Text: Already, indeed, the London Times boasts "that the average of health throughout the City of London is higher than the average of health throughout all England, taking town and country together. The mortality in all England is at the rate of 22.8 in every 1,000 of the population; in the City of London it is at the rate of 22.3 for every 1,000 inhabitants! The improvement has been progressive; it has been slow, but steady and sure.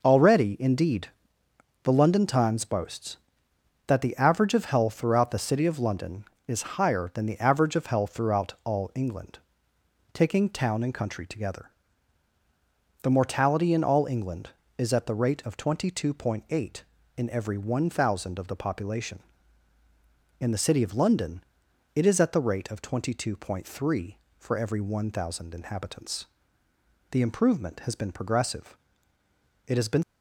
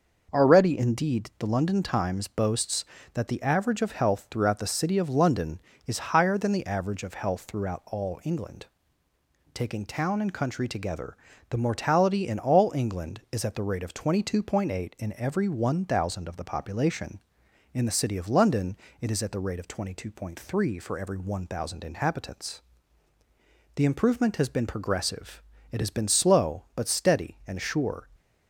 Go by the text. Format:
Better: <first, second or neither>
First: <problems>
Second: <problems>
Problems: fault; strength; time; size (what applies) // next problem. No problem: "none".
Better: second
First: pauses between "London" and "it"; noticeable; at 21.4 s; 0.50 s long // stops before "slow but steady and sure"; at 30.0 s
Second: pauses between "London" and "it"; slight; at 18.7 s; 0.24 s long